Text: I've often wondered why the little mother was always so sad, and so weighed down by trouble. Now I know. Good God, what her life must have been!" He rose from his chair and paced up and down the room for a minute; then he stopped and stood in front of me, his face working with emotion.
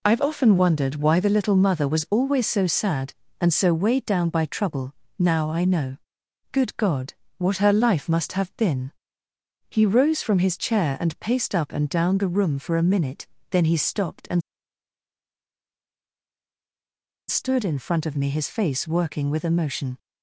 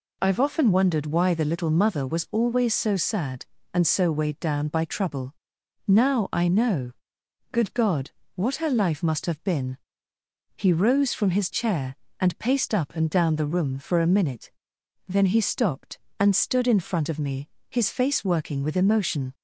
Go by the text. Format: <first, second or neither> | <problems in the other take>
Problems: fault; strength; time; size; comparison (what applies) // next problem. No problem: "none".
second | pauses between "and" and "stood"; strong; at 14.4 s; 2.8 s long